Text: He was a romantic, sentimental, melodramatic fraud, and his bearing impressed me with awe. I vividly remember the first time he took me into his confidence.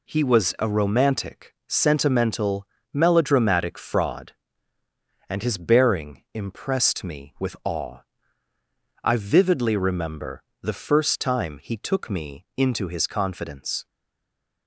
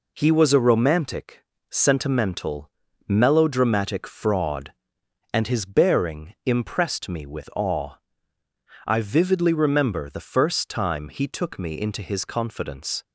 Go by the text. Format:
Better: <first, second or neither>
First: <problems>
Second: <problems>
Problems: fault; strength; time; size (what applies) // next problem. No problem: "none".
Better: second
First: pauses between "remember" and "the"; slight; at 10.4 s; 0.18 s long // stays silent after the last word; slight; from 13.8 s on; 0.8 s long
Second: none